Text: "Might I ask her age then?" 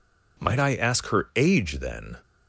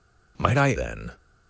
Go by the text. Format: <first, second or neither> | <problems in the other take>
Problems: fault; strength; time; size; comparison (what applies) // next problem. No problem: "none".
first | skips "ask her age"; at 0.7 s